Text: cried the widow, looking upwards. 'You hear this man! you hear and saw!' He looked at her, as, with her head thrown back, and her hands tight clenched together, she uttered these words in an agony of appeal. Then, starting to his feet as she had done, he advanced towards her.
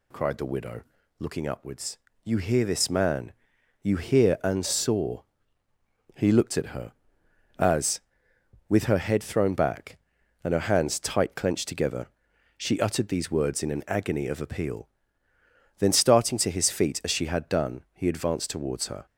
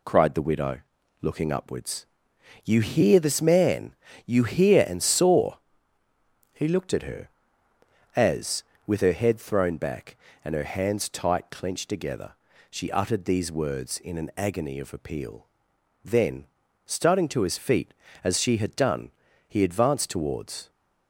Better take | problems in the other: first | stops before "her"; at 20.6 s

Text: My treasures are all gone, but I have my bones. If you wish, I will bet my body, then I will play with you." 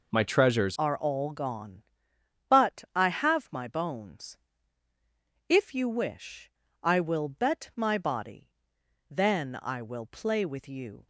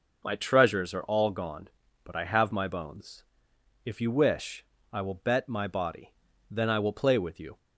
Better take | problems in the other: second | changes voice at "are"; from 0.7 s on; 10.3 s long

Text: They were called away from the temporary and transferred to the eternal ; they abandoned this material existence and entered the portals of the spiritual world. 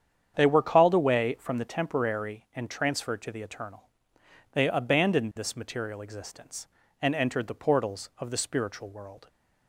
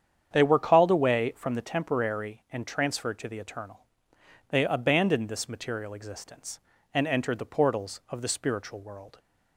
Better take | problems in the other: neither | starts louder than the rest; strong; the same in both

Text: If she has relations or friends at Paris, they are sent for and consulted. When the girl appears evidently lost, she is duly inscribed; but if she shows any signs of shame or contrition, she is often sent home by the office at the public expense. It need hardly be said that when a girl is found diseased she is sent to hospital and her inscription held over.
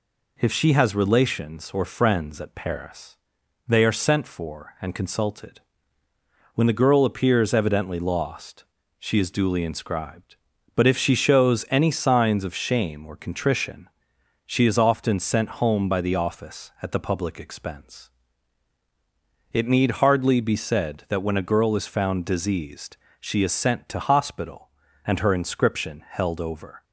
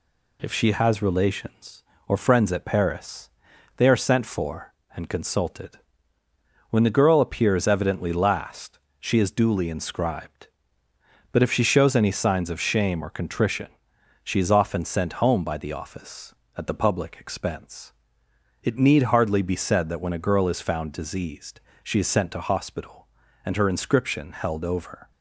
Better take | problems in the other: first | says "last" for "lost"; at 8.1 s // pauses between "diseased" and "she"; slight; at 21.6 s; 0.22 s long; slight in the first

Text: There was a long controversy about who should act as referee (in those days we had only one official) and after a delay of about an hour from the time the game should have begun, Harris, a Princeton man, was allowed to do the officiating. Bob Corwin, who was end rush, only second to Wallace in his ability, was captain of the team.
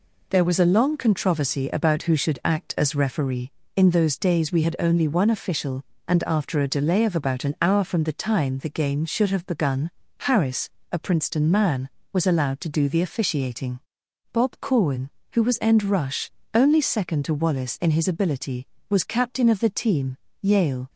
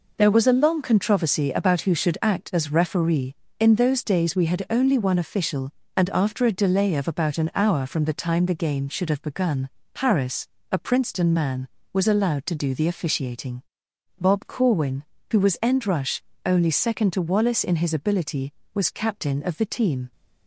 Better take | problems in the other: second | goes on to say "Yale"; slight; from 20.4 s on; 0.48 s long

